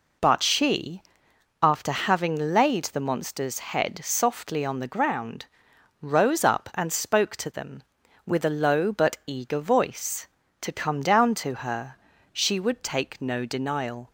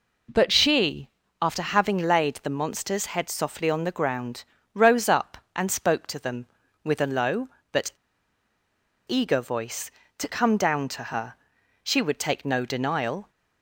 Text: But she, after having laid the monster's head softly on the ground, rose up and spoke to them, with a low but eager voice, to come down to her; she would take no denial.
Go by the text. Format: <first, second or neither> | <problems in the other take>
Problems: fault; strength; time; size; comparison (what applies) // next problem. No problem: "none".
first | pauses between "but" and "eager"; at 7.9 s; 1.1 s long